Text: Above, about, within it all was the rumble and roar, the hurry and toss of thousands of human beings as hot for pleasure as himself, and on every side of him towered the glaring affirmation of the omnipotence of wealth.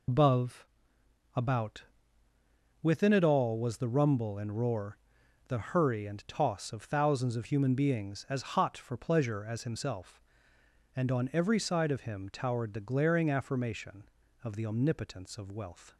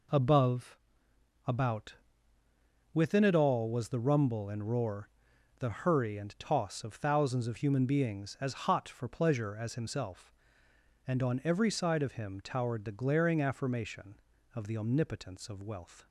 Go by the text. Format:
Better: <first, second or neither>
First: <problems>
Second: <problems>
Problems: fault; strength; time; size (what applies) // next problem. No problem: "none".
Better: second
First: loses the start of "Above"; at 0.0 s; 110 ms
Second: none